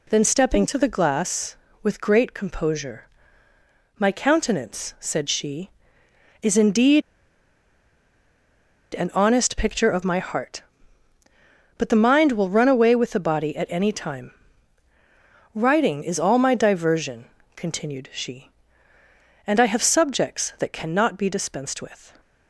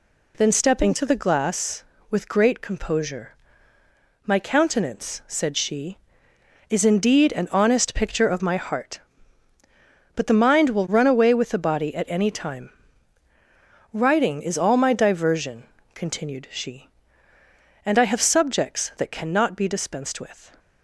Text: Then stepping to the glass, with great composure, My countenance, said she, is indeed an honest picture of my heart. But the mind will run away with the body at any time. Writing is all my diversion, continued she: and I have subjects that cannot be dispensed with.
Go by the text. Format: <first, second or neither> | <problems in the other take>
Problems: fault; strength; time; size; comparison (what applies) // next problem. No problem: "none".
second | pauses between "indeed" and "an"; strong; at 7.0 s; 1.9 s long